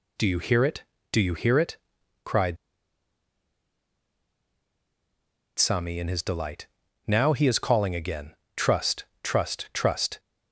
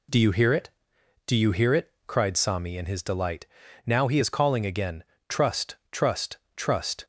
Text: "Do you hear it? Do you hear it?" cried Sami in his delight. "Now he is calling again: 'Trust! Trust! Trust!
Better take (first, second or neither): second